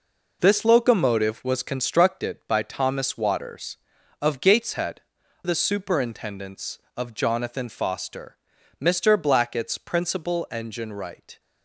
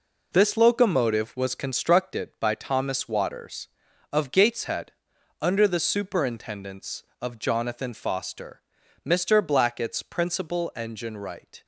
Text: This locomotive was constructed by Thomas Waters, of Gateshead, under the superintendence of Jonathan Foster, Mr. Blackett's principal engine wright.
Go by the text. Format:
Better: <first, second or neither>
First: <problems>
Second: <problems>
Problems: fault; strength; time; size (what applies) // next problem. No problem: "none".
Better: second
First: skips "under"; at 5.2 s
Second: none